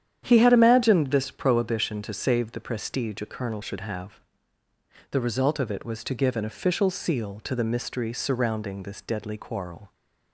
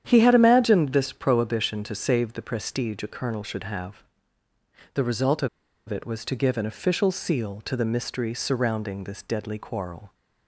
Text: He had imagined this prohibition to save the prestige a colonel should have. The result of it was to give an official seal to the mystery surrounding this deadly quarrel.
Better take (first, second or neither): first